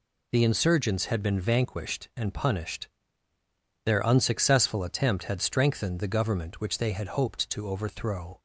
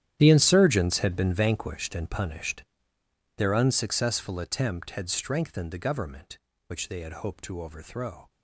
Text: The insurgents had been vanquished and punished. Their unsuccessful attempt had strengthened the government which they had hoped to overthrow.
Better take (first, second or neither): first